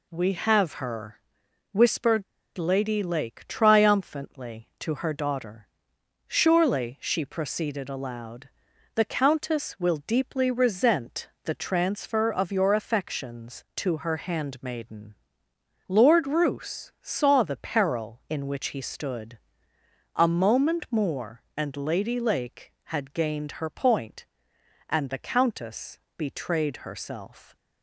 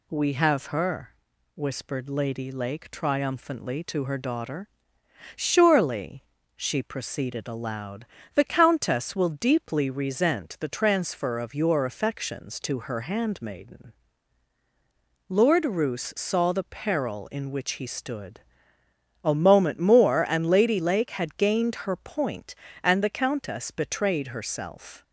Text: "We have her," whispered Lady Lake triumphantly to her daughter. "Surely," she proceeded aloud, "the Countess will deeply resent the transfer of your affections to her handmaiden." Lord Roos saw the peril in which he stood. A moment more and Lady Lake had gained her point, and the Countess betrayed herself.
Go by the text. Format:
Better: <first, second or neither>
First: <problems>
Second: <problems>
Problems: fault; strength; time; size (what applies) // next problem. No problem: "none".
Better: second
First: pauses between "whispered" and "Lady"; slight; at 2.2 s; 0.32 s long // pauses between "resent" and "the"; slight; at 11.2 s; 0.16 s long // pauses between "Countess" and "betrayed"; slight; at 25.9 s; 0.16 s long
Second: none